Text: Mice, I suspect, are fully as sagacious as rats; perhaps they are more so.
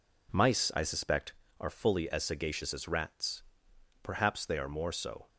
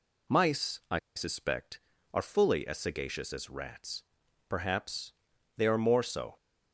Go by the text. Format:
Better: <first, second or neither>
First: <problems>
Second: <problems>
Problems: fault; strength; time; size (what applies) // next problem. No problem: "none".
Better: first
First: none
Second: pauses between "I" and "suspect"; slight; at 0.9 s; 0.18 s long // pauses between "perhaps" and "they"; at 5.1 s; 0.42 s long